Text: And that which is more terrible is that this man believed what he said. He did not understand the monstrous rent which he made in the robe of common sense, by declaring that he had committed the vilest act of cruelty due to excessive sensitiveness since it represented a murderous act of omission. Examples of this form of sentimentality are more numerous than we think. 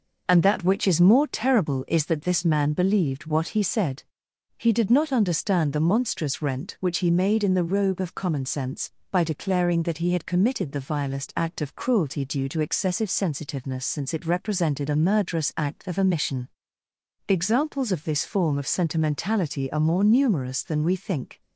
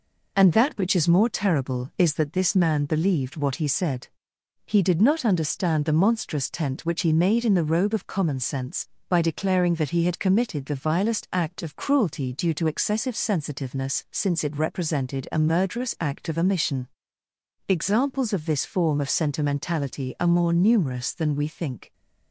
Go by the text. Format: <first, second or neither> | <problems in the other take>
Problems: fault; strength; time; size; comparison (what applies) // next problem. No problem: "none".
first | says "tent" for "rent"; at 6.4 s